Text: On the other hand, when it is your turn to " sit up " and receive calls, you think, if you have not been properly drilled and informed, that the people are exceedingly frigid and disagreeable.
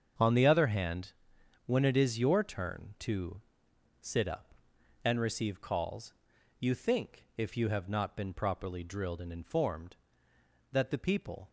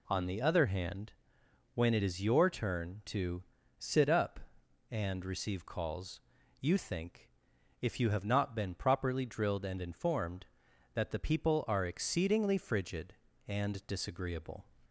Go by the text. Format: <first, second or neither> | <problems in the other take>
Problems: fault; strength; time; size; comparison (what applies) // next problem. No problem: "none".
second | starts louder than the rest; strong; until 1.7 s; 7.5 dB // stops before "are exceedingly frigid and disagreeable"; at 11.4 s